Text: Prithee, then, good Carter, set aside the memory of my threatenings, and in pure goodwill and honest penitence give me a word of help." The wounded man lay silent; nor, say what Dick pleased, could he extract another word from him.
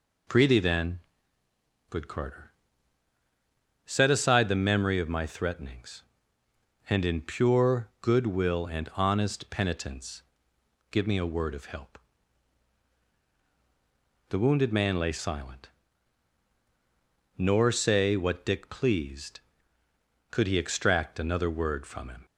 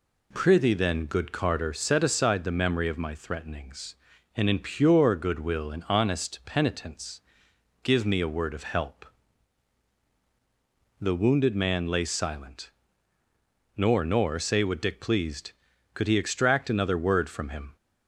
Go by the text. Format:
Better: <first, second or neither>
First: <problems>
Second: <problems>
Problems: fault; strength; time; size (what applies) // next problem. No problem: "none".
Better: first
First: pauses between "penitence" and "give"; noticeable; at 10.2 s; 0.68 s long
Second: pauses between "penitence" and "give"; noticeable; at 7.1 s; 0.64 s long // says "nor" twice; at 14.0 s